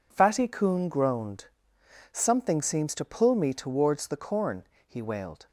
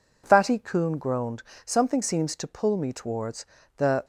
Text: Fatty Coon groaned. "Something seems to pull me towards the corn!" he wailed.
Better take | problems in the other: first | pauses between "towards" and "the"; slight; at 3.4 s; 0.32 s long // stops before "corn he wailed"; at 4.0 s

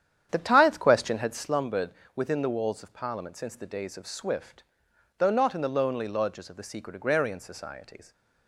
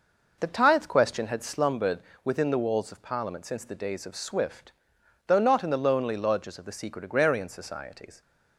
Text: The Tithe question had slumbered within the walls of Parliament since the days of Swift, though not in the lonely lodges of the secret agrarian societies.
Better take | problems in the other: second | starts louder than the rest; strong; until 1.5 s; 9 dB // pauses between "slumbered" and "within"; slight; at 1.9 s; 0.22 s long; slight in the second

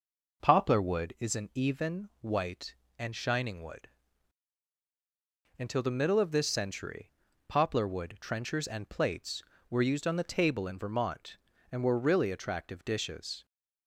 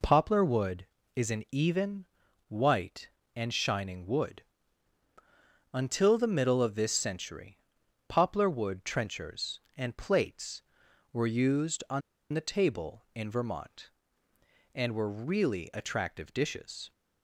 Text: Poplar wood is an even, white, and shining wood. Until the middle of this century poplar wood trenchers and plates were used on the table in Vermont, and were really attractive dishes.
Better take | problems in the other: first | pauses between "century" and "poplar"; noticeable; at 7.5 s; 0.48 s long; also in the first // pauses between "on" and "the"; slight; at 12.0 s; 0.32 s long

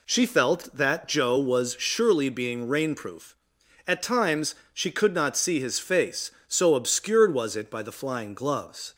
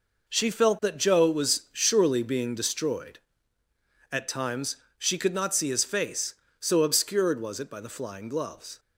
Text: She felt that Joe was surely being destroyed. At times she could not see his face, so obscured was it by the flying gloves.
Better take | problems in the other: second | says "rainproof" for "destroyed"; at 2.6 s // pauses between "times" and "she"; slight; at 4.5 s; 0.18 s long; slight in the second

